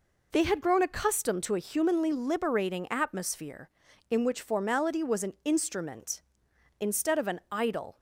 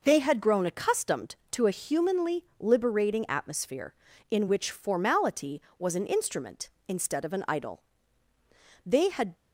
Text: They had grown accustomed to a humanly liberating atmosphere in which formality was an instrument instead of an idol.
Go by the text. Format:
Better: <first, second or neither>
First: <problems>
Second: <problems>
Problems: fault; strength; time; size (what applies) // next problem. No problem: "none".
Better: first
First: none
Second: goes on to say "They had"; from 8.8 s on; 0.50 s long